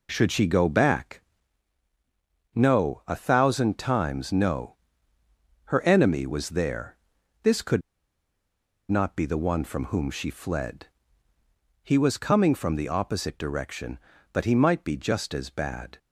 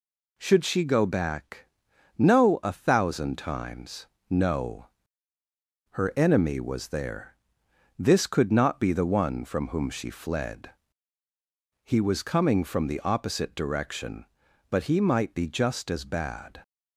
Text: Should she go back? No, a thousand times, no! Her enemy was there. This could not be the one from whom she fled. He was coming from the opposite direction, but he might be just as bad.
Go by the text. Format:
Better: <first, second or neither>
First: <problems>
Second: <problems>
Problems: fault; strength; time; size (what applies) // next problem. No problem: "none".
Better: second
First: pauses between "could" and "not"; at 7.8 s; 1.1 s long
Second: none